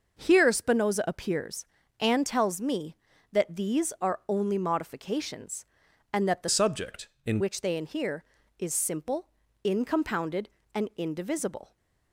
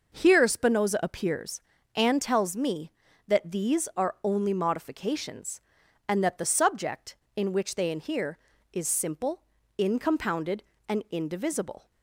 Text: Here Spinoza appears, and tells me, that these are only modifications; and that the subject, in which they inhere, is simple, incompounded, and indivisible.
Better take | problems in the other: second | changes voice from "subject" to "in"; from 6.4 to 7.3 s; 0.9 s long

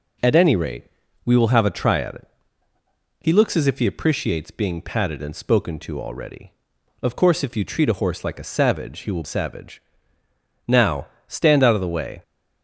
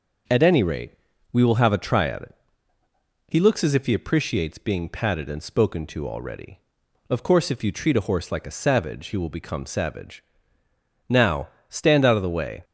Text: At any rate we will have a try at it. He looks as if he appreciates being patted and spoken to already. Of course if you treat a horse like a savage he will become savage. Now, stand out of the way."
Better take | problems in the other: second | pauses between "rate" and "we"; at 0.8 s; 0.38 s long; also in the second // skips "become"; at 9.2 s

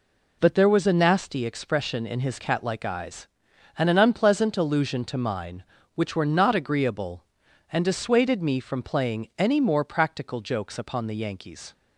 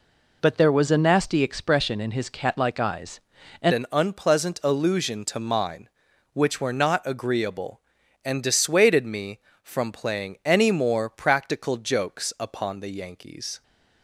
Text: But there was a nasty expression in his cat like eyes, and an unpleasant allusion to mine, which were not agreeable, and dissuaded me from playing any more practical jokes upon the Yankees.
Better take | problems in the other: first | changes voice at "an"; from 3.7 s on; 9.9 s long

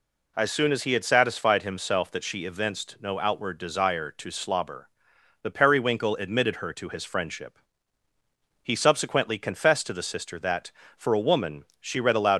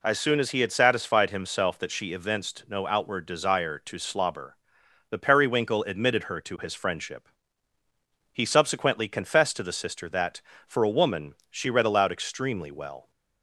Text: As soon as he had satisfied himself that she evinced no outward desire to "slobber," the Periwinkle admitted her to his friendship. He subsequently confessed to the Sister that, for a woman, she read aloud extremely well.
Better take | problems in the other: second | stops before "extremely well"; at 12.3 s

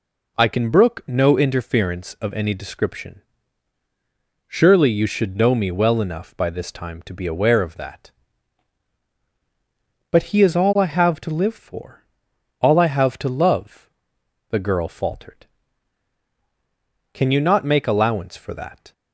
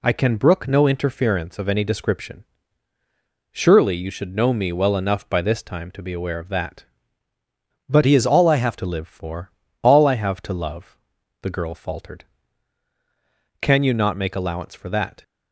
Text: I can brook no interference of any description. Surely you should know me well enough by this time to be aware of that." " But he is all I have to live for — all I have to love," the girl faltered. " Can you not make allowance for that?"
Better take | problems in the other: first | changes voice from "he" to "have"; from 8.0 to 8.7 s; 0.7 s long

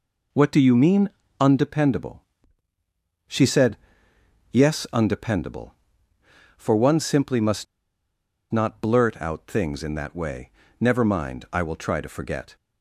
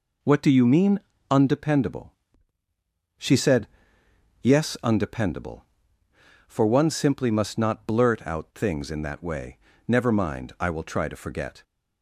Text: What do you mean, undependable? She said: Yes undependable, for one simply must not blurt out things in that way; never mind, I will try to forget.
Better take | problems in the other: second | pauses between "must" and "not"; noticeable; at 7.6 s; 0.86 s long

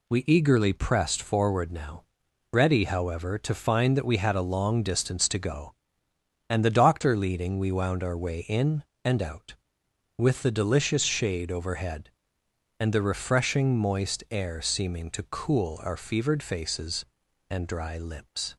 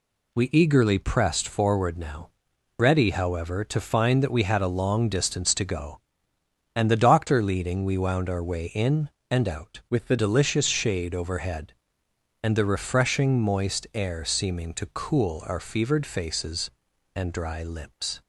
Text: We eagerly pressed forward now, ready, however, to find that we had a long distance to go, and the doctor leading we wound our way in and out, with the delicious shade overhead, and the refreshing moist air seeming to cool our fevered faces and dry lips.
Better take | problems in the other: first | changes voice from "with" to "the"; from 9.8 to 10.1 s; 0.3 s long

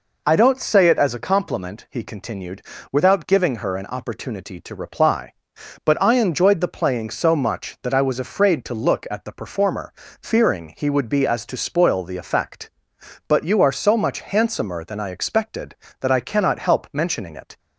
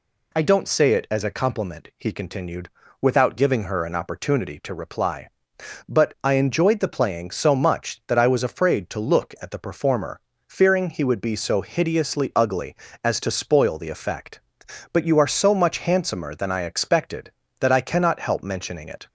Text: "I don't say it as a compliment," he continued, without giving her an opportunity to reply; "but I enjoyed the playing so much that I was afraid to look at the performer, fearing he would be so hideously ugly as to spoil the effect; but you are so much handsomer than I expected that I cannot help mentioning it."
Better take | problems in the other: second | skips "so hideously ugly"; at 11.2 s

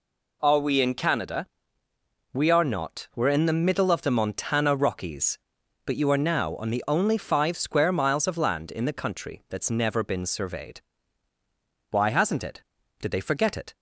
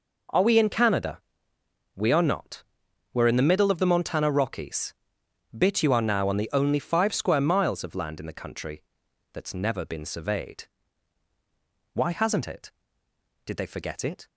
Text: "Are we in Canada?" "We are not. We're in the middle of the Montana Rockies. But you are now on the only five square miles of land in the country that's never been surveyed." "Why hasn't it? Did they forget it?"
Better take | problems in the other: first | says "Bit" for "But"; at 5.5 s // pauses between "country" and "that's"; noticeable; at 8.8 s; 0.48 s long

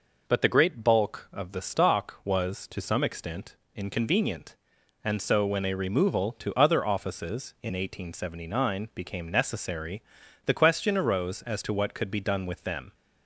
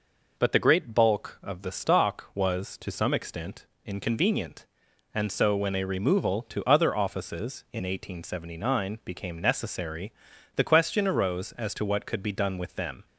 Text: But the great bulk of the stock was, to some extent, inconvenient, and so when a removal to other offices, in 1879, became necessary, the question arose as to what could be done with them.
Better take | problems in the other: neither | none

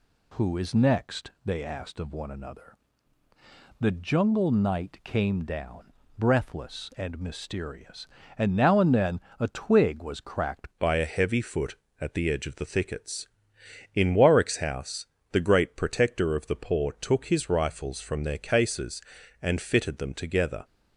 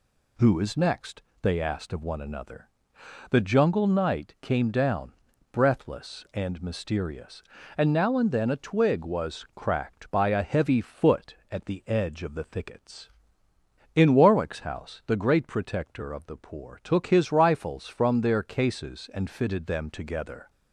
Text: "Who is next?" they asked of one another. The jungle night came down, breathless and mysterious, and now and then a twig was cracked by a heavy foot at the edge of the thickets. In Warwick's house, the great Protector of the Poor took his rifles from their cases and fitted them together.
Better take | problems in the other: second | pauses between "then" and "a"; slight; at 9.2 s; 0.18 s long // changes voice at "by"; from 10.7 s on; 9.9 s long

